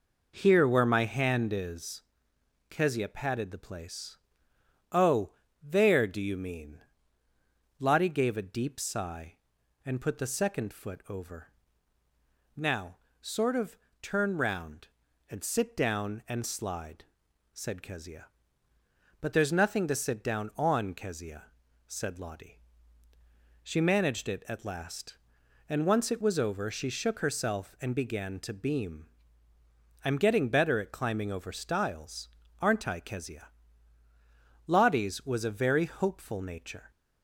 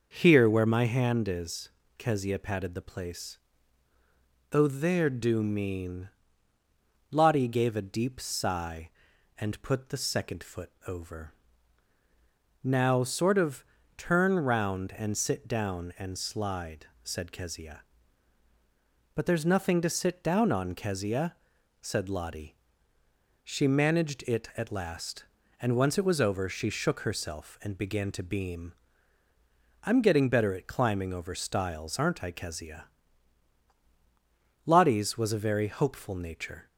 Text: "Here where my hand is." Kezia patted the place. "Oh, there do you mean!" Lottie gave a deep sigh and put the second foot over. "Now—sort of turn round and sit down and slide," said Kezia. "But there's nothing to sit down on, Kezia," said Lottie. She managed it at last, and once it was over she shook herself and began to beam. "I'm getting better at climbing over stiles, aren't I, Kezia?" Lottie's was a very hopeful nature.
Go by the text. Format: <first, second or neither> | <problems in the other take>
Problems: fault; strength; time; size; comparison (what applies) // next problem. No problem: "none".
first | skips "you"; at 5.4 s // pauses between "of" and "turn"; slight; at 13.6 s; 0.34 s long; slight in the first